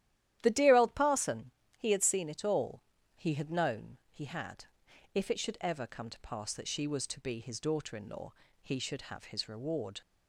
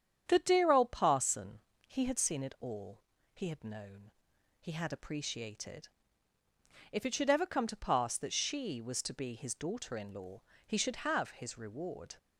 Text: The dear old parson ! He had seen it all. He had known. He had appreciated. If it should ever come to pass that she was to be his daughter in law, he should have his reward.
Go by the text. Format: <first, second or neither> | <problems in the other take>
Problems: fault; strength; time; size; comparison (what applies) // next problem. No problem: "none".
second | starts louder than the rest; strong; until 1.4 s; 12 dB; strong in the second // skips "appreciated"; at 4.8 s